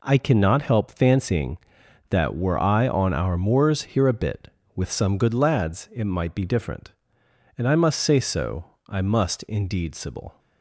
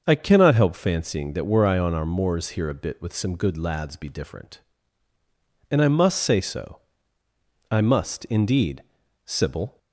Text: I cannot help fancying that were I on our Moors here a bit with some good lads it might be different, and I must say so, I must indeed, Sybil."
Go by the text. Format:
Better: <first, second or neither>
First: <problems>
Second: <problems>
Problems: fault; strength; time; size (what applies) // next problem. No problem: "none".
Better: first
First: none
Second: starts louder than the rest; until 1.0 s; 6.5 dB // skips "it might"; at 3.9 s